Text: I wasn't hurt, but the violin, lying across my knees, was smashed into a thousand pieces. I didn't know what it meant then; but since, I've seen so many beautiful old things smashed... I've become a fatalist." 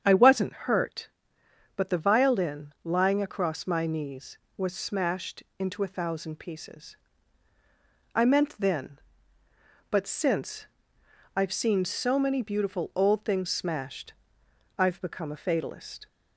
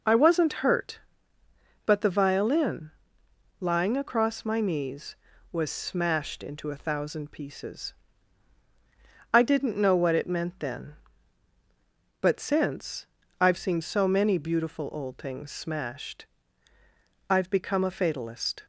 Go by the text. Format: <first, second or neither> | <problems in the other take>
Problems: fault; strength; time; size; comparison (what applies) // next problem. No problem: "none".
second | starts louder than the rest; strong; until 1.0 s; 8 dB // skips "didn't know what it"; at 8.2 s